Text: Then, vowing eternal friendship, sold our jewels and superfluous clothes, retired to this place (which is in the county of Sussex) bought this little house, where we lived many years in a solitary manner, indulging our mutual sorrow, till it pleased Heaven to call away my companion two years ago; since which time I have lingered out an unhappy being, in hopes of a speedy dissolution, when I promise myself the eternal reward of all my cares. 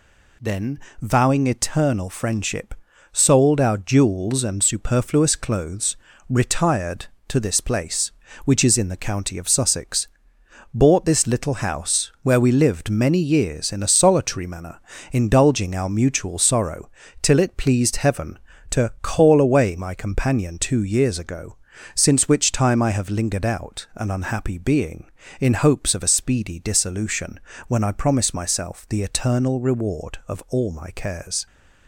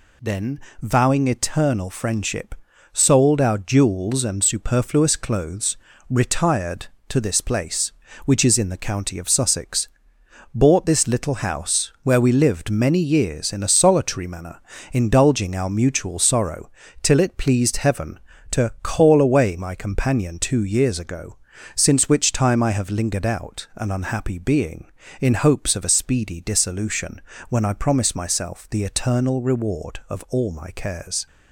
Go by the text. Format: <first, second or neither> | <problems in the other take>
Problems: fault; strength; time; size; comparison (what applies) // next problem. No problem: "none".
neither | none